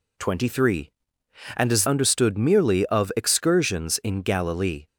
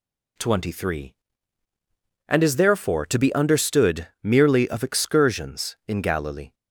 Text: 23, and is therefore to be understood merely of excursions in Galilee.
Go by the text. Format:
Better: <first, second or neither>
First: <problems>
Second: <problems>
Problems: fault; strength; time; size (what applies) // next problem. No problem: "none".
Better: second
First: skips "therefore to be"; at 1.8 s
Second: none